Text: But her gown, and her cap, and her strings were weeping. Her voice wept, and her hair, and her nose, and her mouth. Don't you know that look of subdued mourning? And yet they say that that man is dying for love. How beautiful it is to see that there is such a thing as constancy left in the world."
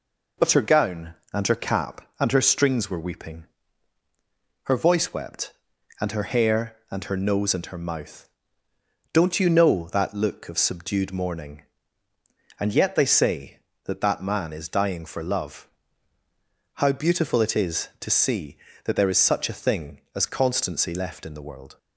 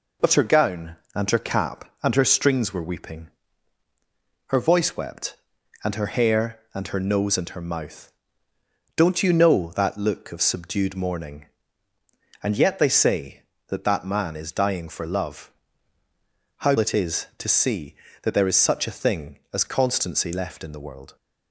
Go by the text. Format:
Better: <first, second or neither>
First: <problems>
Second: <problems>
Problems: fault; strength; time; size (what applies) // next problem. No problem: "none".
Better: first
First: none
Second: skips "beautiful"; at 16.7 s